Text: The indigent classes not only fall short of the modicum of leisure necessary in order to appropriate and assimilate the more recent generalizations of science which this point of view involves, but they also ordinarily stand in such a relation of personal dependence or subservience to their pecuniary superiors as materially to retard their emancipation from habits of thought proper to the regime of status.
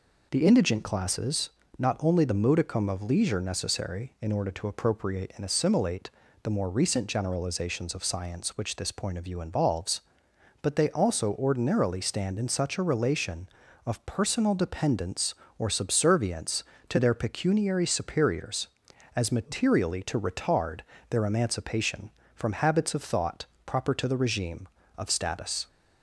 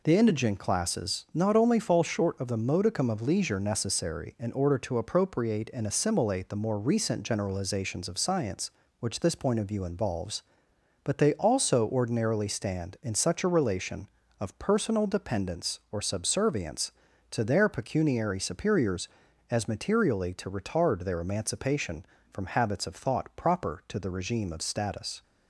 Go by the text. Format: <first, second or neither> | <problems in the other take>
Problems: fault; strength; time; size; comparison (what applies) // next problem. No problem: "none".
second | pauses between "classes" and "not"; slight; at 1.5 s; 0.28 s long // skips "fall short of"; at 2.2 s // pauses between "assimilate" and "the"; slight; at 6.0 s; 0.34 s long // pauses between "retard" and "their"; slight; at 20.8 s; 0.30 s long // pauses between "thought" and "proper"; slight; at 23.4 s; 0.20 s long